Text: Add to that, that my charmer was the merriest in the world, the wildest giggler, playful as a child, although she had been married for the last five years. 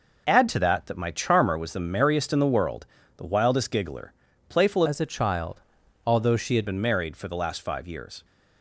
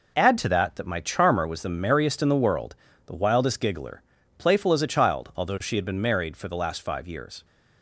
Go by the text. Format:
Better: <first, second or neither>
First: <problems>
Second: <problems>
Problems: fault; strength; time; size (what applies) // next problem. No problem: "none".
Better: second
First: changes voice from "as" to "had"; from 4.8 to 6.6 s; 1.8 s long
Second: none